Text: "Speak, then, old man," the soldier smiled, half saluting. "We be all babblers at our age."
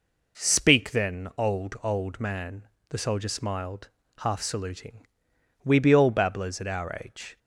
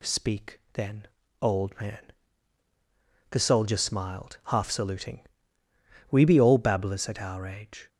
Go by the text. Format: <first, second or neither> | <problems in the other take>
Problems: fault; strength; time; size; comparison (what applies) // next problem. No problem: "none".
second | says "old" twice; at 1.8 s